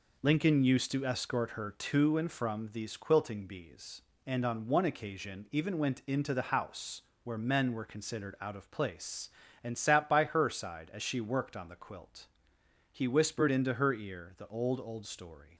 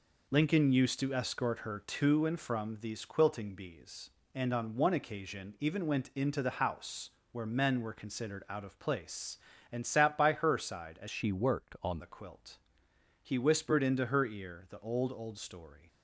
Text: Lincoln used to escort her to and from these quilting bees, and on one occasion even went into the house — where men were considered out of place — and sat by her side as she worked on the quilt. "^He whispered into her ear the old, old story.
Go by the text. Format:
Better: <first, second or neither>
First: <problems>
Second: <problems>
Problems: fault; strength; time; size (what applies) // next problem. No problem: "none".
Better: first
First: none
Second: changes voice from "she" to "on"; from 11.0 to 11.9 s; 0.9 s long